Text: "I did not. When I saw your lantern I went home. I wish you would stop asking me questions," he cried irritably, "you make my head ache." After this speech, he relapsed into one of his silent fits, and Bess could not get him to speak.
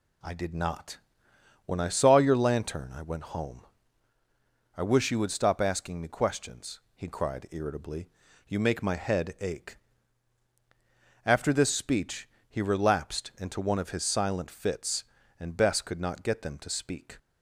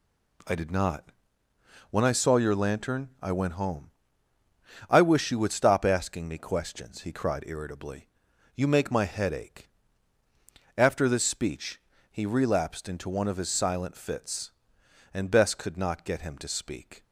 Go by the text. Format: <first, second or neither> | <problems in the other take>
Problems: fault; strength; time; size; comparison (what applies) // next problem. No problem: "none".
second | says "them" for "him"; at 16.4 s